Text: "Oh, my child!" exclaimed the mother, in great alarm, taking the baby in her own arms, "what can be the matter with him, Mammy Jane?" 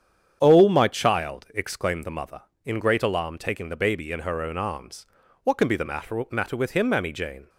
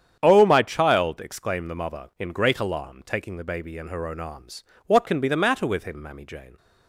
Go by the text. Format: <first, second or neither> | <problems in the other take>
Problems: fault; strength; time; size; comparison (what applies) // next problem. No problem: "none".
second | starts louder than the rest; strong; until 1.4 s; 8 dB; strong in the second // says "matter" twice; at 6.3 s